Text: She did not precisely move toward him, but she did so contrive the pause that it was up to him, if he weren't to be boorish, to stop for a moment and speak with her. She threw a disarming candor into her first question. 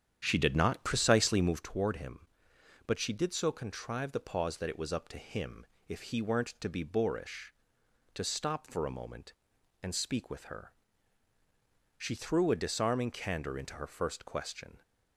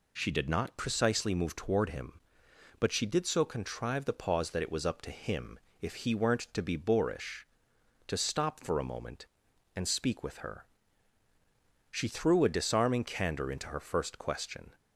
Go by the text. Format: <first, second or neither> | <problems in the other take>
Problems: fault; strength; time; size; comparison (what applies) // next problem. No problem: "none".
second | starts louder than the rest; strong; until 1.6 s; 8.5 dB